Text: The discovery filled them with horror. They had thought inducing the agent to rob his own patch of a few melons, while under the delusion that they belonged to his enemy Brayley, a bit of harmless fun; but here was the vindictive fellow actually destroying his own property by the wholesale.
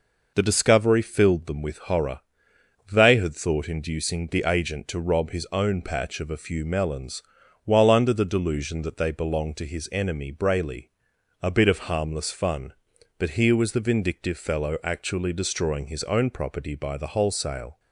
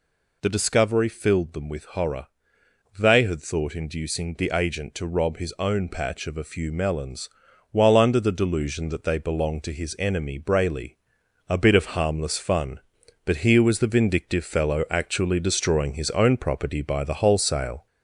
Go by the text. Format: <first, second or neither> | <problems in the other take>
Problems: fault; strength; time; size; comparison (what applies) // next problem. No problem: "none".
first | gets louder; slight; throughout; 3 dB